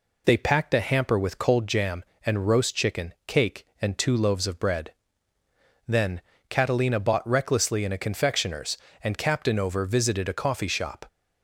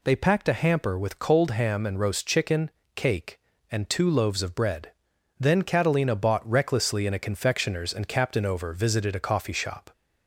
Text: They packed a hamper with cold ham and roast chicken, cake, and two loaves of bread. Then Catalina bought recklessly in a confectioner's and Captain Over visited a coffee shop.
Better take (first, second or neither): second